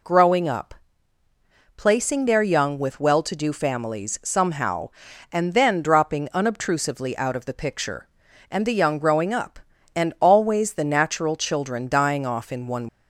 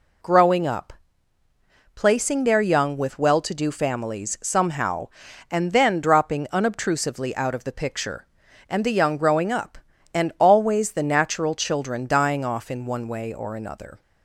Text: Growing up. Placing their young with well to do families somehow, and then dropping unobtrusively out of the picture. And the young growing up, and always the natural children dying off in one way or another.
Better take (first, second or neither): second